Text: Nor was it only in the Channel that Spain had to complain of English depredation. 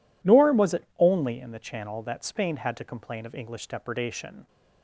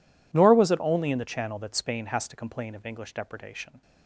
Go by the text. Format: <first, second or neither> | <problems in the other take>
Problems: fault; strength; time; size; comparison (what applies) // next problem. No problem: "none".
first | says "has" for "had"; at 2.0 s